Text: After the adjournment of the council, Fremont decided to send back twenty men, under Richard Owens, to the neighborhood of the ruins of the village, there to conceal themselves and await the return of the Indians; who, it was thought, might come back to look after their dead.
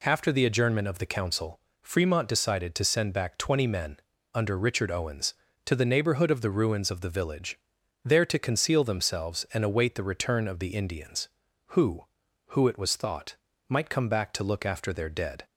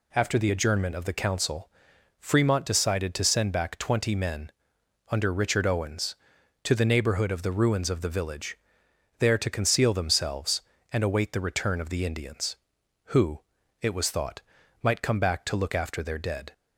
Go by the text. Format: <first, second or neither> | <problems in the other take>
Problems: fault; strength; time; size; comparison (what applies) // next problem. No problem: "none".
second | says "who" twice; at 12.4 s